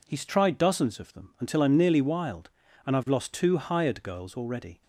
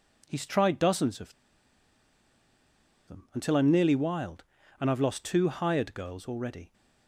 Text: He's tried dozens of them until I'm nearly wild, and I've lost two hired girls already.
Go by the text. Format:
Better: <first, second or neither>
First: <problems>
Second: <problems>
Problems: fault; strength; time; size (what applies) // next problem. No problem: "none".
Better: first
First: none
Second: pauses between "of" and "them"; strong; at 1.3 s; 1.7 s long